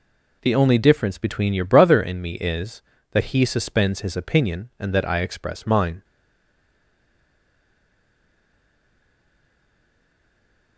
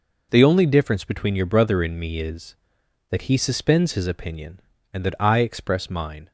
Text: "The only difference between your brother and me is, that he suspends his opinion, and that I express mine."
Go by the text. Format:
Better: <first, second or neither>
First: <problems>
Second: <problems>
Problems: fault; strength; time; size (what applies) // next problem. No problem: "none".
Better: second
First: stays silent after the last word; strong; from 6.0 s on; 4.7 s long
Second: none